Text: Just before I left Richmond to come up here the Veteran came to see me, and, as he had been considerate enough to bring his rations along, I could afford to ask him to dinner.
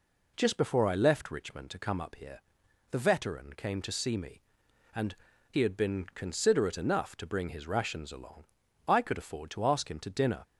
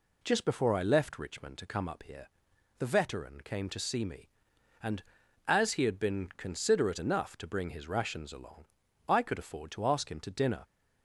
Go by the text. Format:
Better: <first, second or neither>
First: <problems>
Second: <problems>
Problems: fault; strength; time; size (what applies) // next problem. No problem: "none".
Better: second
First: pauses between "here" and "the"; noticeable; at 2.3 s; 0.50 s long // skips "as"; at 5.3 s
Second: pauses between "here" and "the"; noticeable; at 2.2 s; 0.50 s long